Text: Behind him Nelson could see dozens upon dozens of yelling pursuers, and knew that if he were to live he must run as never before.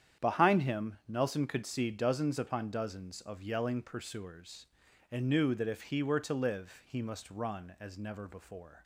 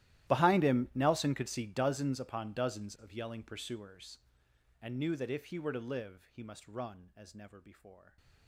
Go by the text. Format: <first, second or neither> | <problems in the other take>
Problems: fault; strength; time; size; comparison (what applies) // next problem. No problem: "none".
first | gets quieter; strong; throughout; 23.5 dB // starts louder than the rest; strong; until 1.3 s; 14.5 dB; strong in the first